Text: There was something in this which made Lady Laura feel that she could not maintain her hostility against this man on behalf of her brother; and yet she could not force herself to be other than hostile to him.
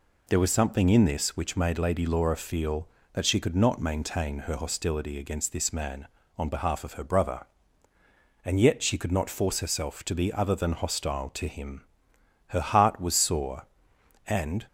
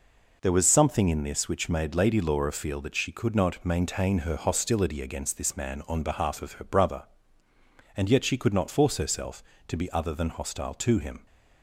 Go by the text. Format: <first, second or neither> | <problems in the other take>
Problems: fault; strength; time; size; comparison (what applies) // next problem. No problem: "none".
second | goes on to say "Her heart was sore and"; strong; from 12.4 s on; 2.1 s long